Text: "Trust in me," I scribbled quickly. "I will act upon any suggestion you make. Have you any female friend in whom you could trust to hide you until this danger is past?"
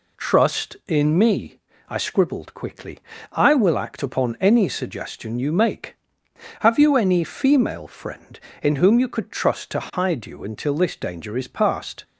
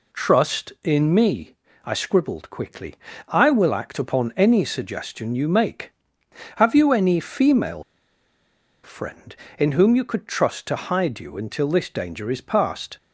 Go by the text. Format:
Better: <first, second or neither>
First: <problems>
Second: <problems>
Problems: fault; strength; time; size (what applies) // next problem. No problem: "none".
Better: first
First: none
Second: pauses between "female" and "friend"; at 7.8 s; 1.0 s long